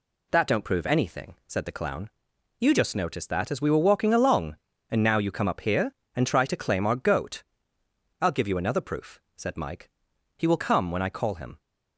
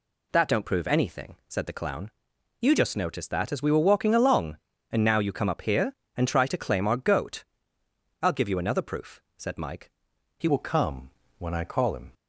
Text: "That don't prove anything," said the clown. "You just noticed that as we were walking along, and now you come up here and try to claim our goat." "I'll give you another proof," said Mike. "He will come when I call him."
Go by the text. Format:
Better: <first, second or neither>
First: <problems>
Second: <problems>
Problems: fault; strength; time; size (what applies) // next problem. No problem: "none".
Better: first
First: none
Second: changes voice at "will"; from 10.4 s on; 1.7 s long // pauses between "come" and "when"; slight; at 11.0 s; 0.28 s long